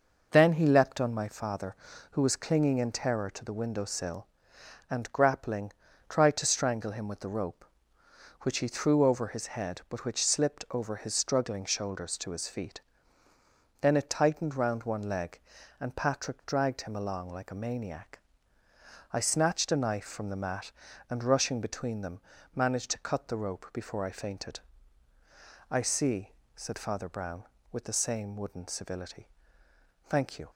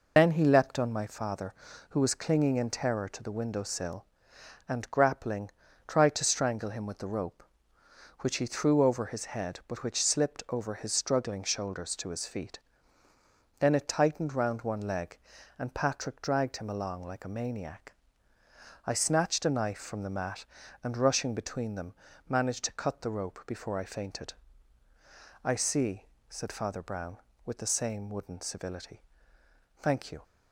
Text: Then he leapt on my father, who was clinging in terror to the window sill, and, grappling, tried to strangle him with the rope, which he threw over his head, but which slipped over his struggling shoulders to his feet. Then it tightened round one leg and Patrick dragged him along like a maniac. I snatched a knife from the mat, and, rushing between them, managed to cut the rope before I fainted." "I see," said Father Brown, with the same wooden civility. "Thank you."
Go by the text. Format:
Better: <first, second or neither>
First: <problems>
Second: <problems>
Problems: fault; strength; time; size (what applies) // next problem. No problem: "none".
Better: first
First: none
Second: loses the start of "Then"; at 0.1 s; 70 ms